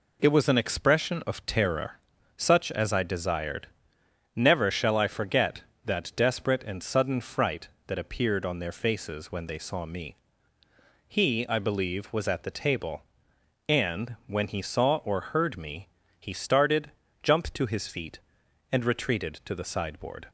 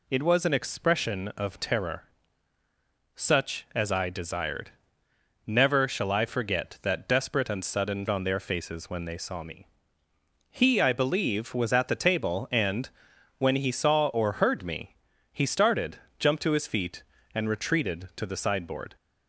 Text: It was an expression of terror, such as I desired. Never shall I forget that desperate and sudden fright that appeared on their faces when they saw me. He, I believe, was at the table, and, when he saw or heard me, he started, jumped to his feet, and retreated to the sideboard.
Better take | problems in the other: first | skips "fright that appeared"; at 8.0 s

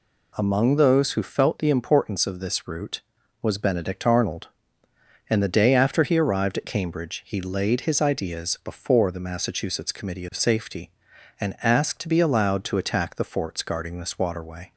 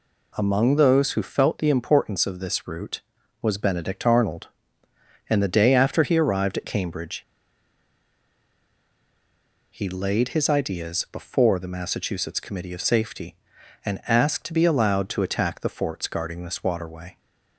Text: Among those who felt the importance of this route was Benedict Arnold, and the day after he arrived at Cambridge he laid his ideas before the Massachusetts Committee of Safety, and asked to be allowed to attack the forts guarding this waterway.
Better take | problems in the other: first | pauses between "Cambridge" and "he"; strong; at 7.2 s; 2.5 s long

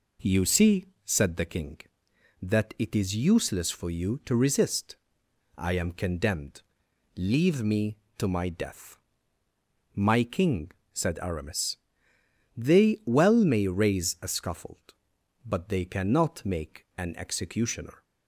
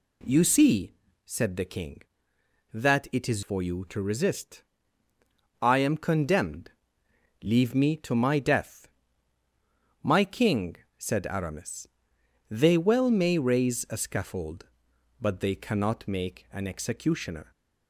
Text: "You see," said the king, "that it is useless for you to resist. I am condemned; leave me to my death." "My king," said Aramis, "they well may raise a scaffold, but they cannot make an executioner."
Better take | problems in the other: first | skips "useless"; at 3.4 s

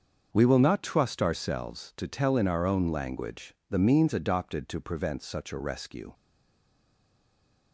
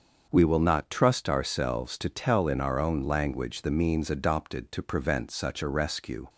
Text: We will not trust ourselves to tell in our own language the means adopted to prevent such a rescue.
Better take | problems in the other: second | starts louder than the rest; until 1.3 s; 6.5 dB; also in the second // pauses between "language" and "the"; slight; at 3.5 s; 0.16 s long // stays silent after the last word; noticeable; from 6.1 s on; 1.6 s long

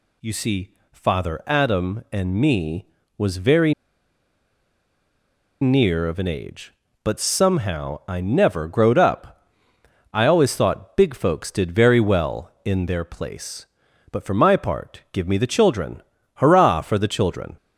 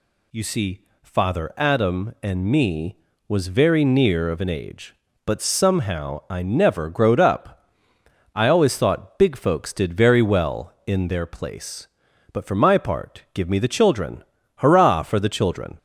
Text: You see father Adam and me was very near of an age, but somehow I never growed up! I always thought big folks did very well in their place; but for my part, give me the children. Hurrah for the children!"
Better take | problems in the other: second | pauses between "see" and "father"; slight; at 0.7 s; 0.18 s long; slight in the second // pauses between "very" and "near"; strong; at 3.7 s; 1.8 s long

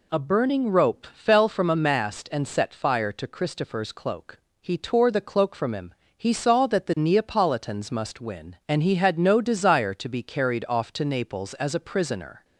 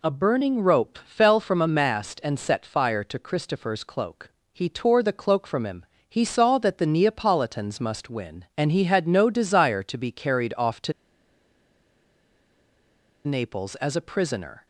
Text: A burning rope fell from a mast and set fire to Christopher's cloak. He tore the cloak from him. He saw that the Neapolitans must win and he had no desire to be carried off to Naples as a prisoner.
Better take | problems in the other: first | pauses between "to" and "Naples"; strong; at 10.9 s; 2.3 s long

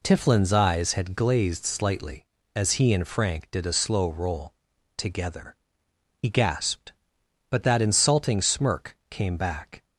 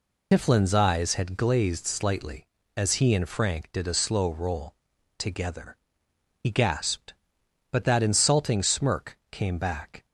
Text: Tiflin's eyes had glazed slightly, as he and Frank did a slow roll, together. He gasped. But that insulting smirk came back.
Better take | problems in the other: first | loses the start of "Tiflin's"; at 0.3 s; 65 ms

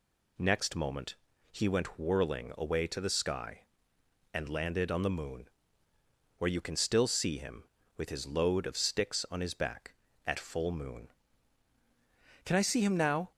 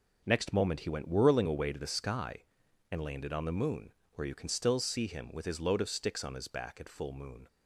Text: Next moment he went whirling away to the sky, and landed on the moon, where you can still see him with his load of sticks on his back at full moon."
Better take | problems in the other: second | pauses between "moment" and "he"; slight; at 1.1 s; 0.34 s long // goes on to say "Can I see him now"; noticeable; from 12.4 s on; 0.86 s long

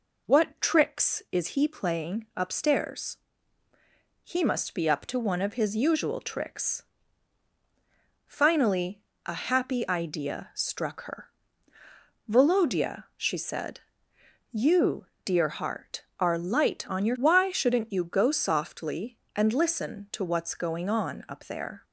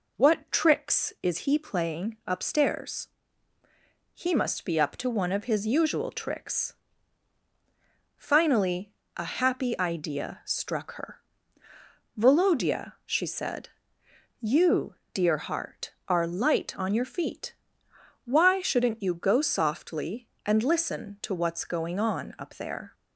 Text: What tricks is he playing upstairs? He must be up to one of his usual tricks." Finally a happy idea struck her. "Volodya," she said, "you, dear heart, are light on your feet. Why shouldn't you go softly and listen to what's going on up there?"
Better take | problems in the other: second | pauses between "Finally" and "a"; slight; at 9.0 s; 0.26 s long; slight in the second // skips "feet"; at 17.1 s

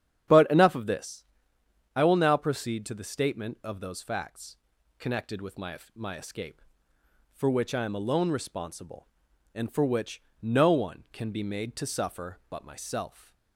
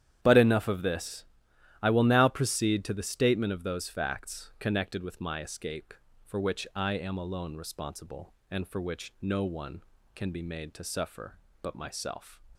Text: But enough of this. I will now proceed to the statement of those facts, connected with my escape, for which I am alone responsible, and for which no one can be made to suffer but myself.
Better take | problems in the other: second | starts louder than the rest; strong; until 2.0 s; 9 dB; strong in the second // says "my" twice; at 5.9 s // pauses between "which" and "no"; slight; at 10.2 s; 0.18 s long

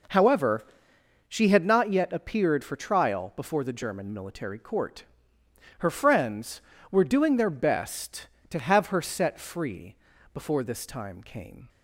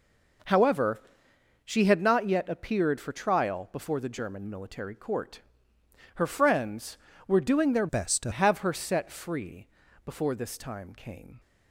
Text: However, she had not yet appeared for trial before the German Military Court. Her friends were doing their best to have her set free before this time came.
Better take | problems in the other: first | changes voice from "best" to "to"; from 7.8 to 8.3 s; 0.5 s long // pauses between "free" and "before"; slight; at 9.6 s; 0.36 s long; slight in the first

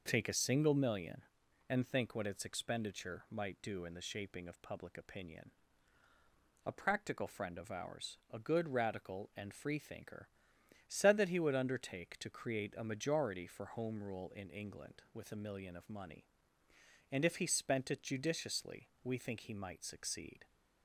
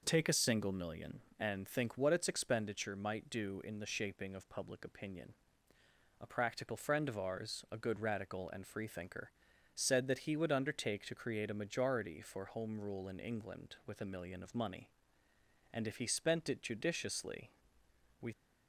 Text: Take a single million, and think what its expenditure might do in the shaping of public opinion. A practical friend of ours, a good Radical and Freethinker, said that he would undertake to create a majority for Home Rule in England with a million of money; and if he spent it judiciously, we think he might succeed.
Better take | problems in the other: first | stops before "think he might succeed"; at 18.3 s

